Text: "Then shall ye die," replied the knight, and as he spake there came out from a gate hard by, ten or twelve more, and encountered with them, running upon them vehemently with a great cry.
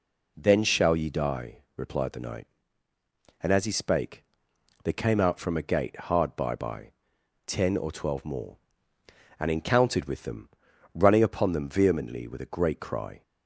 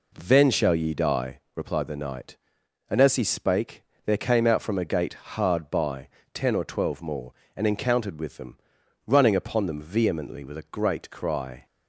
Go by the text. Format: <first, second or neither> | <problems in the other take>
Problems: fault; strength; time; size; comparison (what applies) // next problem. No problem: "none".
second | pauses between "spake" and "there"; noticeable; at 4.2 s; 0.58 s long; slight in the second // says "by" twice; at 6.5 s